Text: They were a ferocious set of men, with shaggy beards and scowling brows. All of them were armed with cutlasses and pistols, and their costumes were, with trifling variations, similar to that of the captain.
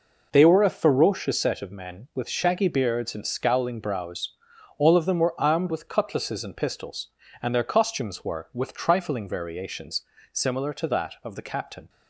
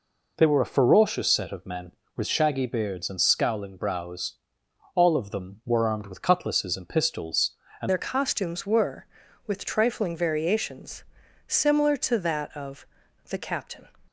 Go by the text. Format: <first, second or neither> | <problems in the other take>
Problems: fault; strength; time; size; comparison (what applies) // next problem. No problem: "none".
first | changes voice at "their"; from 7.8 s on; 6.0 s long // pauses between "of" and "the"; at 12.8 s; 0.44 s long